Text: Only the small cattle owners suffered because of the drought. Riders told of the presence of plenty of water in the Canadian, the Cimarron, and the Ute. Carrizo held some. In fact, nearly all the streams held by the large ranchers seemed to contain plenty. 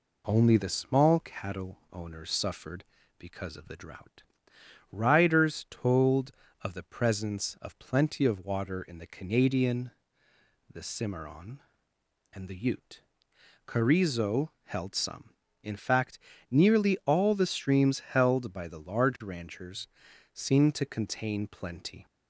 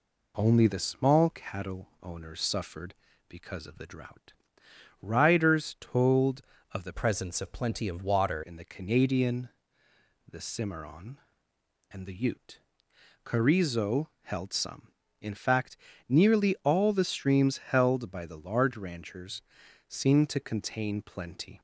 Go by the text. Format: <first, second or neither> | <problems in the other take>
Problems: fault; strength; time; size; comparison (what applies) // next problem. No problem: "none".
first | changes voice from "presence" to "water"; from 6.9 to 8.4 s; 1.5 s long // pauses between "ranchers" and "seemed"; at 19.4 s; 0.44 s long; also in the first